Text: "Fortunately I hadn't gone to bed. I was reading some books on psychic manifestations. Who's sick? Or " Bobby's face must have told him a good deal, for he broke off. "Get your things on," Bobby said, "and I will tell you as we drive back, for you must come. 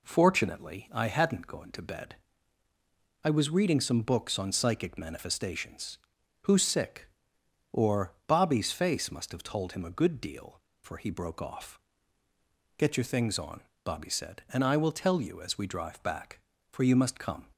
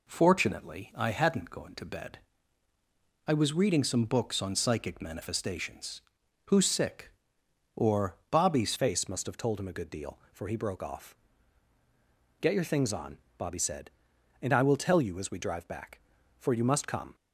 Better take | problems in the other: first | changes voice at "face"; from 8.7 s on; 8.4 s long

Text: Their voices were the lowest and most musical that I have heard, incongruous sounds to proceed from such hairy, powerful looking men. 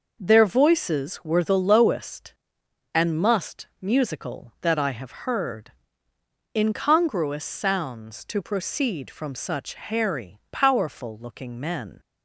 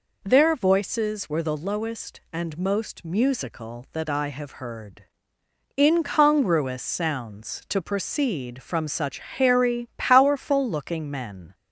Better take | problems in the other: second | says "must" for "most"; at 3.1 s

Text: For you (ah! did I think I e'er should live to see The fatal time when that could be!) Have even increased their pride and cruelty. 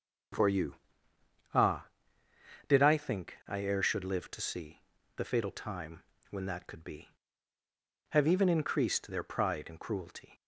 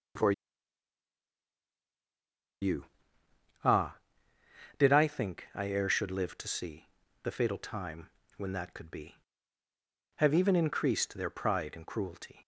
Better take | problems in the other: first | starts louder than the rest; strong; until 5.0 s; 8 dB; strong in the first // pauses between "For" and "you"; strong; at 0.3 s; 2.2 s long // pauses between "see" and "The"; slight; at 6.8 s; 0.32 s long; slight in the first // pauses between "time" and "when"; slight; at 8.0 s; 0.26 s long; slight in the first

